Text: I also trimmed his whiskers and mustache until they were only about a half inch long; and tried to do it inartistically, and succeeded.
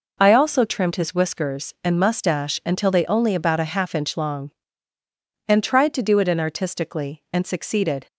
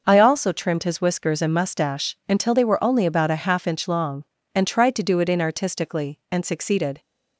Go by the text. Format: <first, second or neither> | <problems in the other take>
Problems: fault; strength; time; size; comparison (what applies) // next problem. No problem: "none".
second | skips "were"; at 3.0 s